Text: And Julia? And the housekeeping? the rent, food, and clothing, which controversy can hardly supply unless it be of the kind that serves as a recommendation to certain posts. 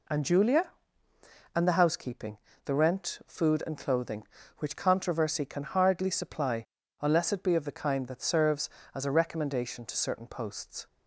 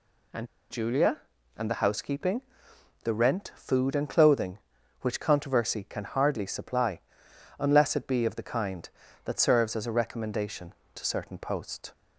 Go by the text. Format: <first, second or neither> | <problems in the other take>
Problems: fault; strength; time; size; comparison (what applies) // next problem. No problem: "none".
first | pauses between "And" and "Julia"; slight; at 0.4 s; 0.24 s long // pauses between "supply" and "unless"; noticeable; at 6.9 s; 0.58 s long; slight in the first